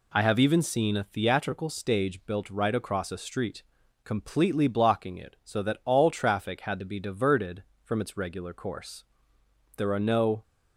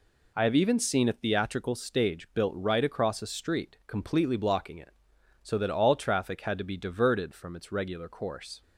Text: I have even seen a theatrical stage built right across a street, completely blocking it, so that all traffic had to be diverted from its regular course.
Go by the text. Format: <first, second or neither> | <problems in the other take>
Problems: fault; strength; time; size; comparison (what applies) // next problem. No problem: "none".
second | goes on to say "There are no"; noticeable; from 9.7 s on; 0.66 s long